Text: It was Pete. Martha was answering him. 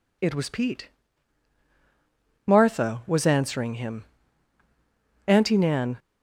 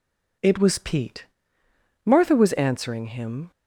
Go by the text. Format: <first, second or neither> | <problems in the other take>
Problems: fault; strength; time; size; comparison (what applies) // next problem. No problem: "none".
second | goes on to say "Auntie Nan"; noticeable; from 5.2 s on; 0.72 s long